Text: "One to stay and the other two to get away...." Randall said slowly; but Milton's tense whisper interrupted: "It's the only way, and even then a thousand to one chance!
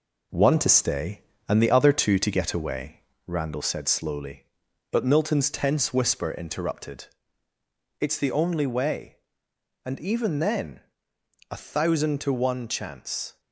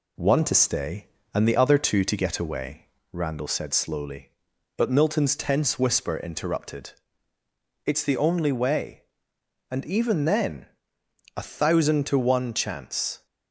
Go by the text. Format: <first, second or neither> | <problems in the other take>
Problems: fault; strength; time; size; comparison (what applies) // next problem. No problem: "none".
second | gets quieter; noticeable; throughout; 5 dB // pauses between "then" and "a"; noticeable; at 10.8 s; 0.68 s long; noticeable in the second